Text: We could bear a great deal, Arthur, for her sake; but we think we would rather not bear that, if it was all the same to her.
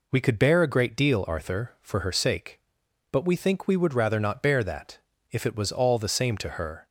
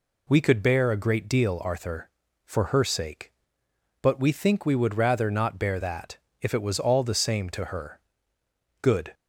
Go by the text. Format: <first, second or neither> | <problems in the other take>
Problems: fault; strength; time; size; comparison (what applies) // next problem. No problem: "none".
first | goes on to say "Good"; slight; from 8.7 s on; 0.34 s long